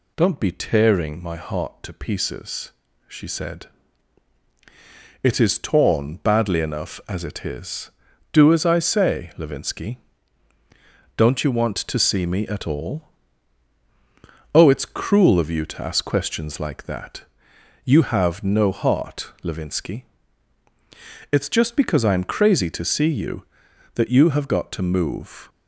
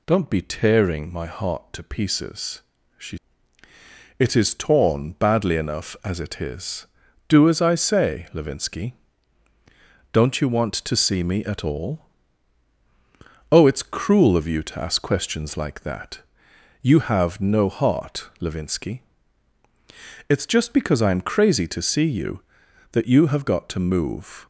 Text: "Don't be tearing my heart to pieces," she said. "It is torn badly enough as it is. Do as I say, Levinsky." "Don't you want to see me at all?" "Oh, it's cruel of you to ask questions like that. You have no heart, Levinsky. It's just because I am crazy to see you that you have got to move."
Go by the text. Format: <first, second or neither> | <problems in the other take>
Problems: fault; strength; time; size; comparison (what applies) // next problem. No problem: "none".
first | skips "said"; at 3.6 s